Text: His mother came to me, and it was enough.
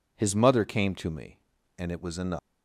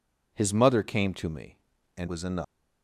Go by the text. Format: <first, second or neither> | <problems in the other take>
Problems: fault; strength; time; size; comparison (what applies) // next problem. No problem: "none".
first | skips "it"; at 2.0 s